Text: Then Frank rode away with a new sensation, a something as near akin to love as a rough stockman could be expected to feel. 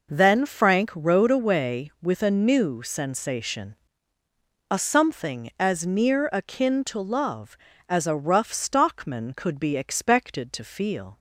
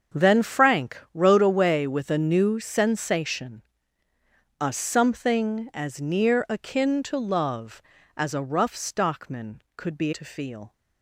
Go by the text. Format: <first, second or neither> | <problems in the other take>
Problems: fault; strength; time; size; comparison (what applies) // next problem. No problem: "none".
first | starts louder than the rest; strong; until 1.3 s; 7.5 dB // pauses between "Frank" and "rode"; slight; at 0.9 s; 0.16 s long // skips "expected"; at 10.1 s